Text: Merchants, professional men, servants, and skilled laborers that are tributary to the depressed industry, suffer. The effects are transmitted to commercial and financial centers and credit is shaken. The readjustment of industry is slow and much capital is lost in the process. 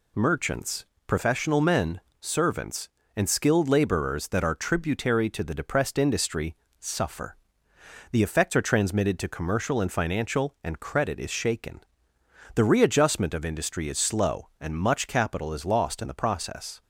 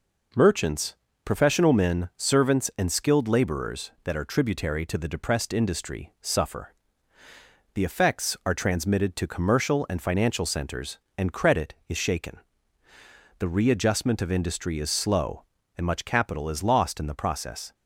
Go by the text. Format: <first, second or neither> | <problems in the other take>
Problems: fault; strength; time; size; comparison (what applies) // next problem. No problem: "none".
second | skips "centers"; at 10.5 s